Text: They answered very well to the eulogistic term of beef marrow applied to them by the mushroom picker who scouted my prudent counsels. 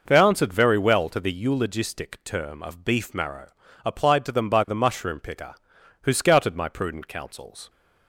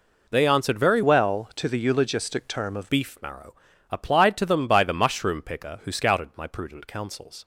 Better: first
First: pauses between "marrow" and "applied"; slight; at 3.4 s; 0.36 s long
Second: changes voice from "well" to "of"; from 1.0 to 2.9 s; 1.9 s long // pauses between "marrow" and "applied"; slight; at 3.5 s; 0.36 s long

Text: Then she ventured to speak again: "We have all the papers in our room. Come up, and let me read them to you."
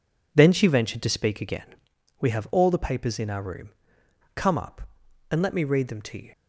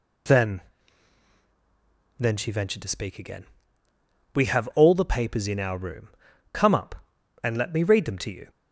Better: first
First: none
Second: says "Then" twice; at 2.1 s

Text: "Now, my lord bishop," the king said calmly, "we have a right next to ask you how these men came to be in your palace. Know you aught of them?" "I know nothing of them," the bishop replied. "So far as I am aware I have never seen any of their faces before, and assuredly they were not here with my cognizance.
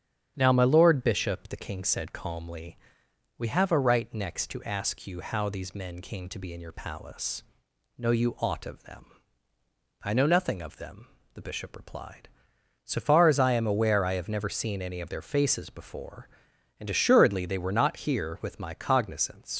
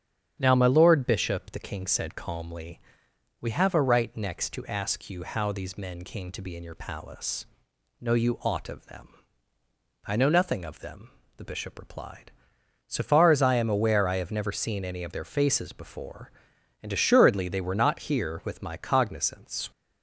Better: second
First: starts louder than the rest; strong; until 1.3 s; 9 dB // leaves "cognizance" unfinished; at 19.5 s; 85 ms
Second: starts louder than the rest; strong; until 1.3 s; 9 dB

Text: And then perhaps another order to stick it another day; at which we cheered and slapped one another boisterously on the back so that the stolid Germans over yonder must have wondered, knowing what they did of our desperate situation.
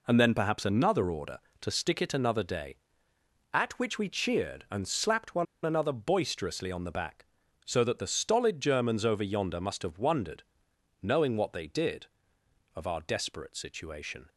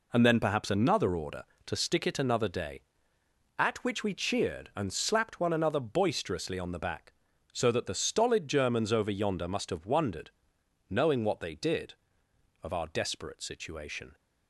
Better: second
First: pauses between "one" and "another"; slight; at 5.4 s; 0.20 s long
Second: none

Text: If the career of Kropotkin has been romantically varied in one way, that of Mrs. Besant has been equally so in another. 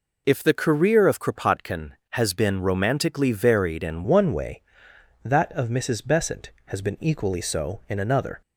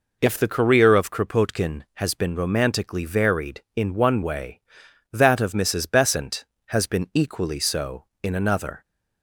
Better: second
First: changes voice at "one"; from 4.0 s on; 4.4 s long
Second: none

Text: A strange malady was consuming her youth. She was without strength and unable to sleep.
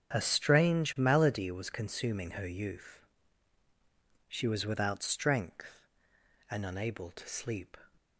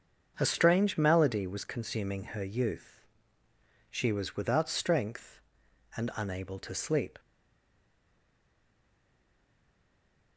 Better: first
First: starts louder than the rest; strong; until 1.1 s; 8 dB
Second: starts louder than the rest; until 1.3 s; 7 dB // stays silent after the last word; strong; from 7.1 s on; 3.2 s long

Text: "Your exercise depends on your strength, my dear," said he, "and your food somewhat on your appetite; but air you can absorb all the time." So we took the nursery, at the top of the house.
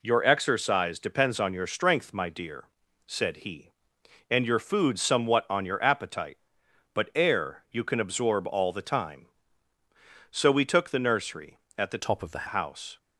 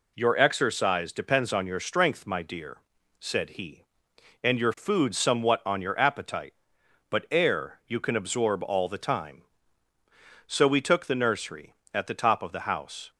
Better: second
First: changes voice from "top" to "the"; from 12.0 to 12.4 s; 0.4 s long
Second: none

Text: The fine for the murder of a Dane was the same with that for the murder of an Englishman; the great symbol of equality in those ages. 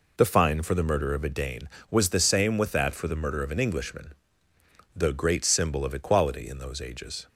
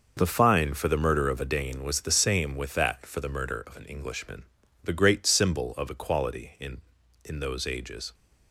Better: first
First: none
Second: says "in" twice; at 7.2 s

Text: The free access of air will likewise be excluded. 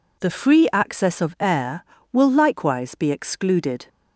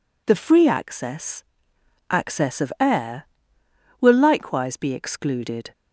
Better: first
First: none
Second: says "access" twice; at 2.0 s

